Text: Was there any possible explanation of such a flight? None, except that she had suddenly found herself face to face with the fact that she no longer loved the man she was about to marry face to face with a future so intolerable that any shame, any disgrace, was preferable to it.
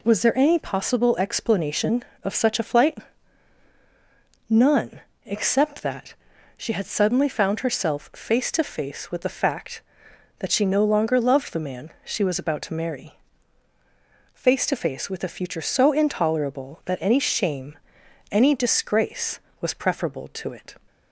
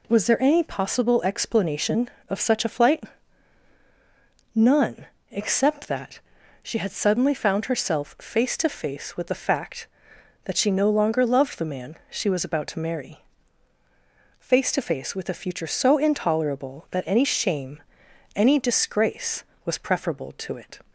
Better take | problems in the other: neither | pauses between "that" and "she"; the same in both // pauses between "marry" and "face"; the same in both

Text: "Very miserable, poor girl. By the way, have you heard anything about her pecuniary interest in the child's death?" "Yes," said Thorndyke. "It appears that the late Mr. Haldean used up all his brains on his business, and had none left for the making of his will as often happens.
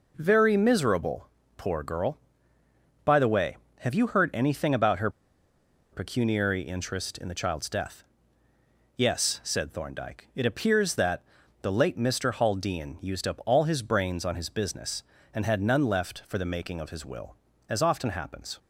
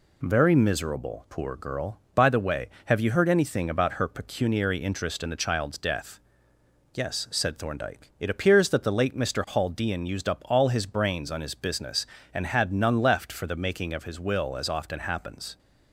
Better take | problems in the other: second | pauses between "her" and "pecuniary"; noticeable; at 5.0 s; 0.83 s long // pauses between "that" and "the"; at 11.2 s; 0.38 s long

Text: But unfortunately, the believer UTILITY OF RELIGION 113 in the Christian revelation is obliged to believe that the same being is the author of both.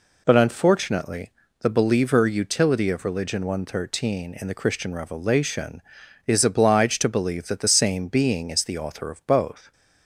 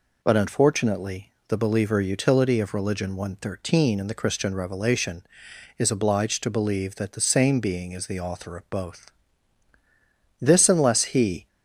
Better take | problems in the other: first | goes on to say "This unless he"; noticeable; from 10.4 s on; 1.0 s long

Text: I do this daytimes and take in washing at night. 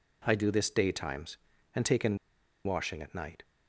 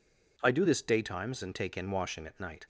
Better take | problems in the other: second | pauses between "in" and "washing"; noticeable; at 2.1 s; 0.48 s long

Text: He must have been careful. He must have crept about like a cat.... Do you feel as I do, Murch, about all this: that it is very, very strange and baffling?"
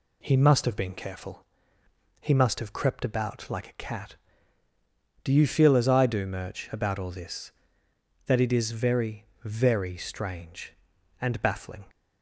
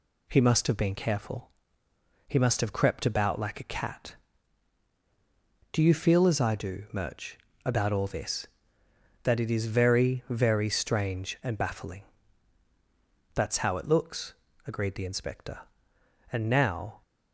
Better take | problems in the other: first | goes on to say "That's how it looks agreed the inspector And now"; strong; from 13.3 s on; 3.6 s long

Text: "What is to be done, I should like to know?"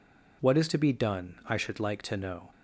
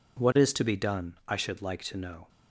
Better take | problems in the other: neither | none

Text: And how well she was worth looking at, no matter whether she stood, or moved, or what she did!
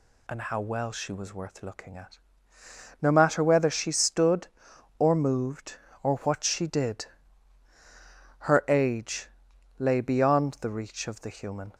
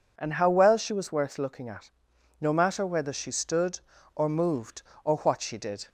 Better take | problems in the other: second | goes on to say "Her age lay beyond the reach of the human"; strong; from 8.3 s on; 3.3 s long

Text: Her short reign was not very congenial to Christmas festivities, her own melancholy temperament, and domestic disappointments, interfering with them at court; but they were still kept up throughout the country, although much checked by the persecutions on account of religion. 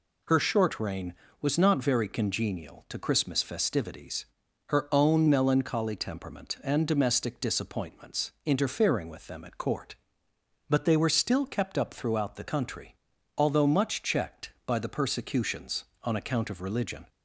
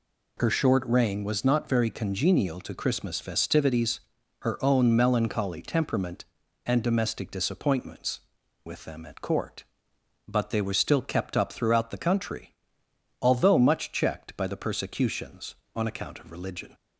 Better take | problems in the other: first | skips "interfering"; at 8.4 s

